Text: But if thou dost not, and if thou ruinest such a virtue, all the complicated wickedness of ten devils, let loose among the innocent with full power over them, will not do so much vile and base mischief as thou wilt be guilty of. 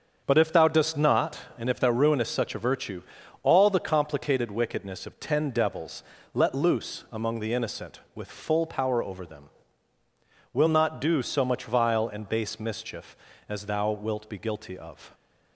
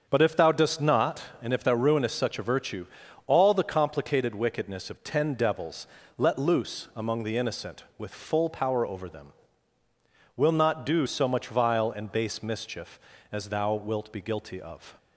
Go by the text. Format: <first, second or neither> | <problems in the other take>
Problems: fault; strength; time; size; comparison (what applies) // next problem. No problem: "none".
neither | starts louder than the rest; the same in both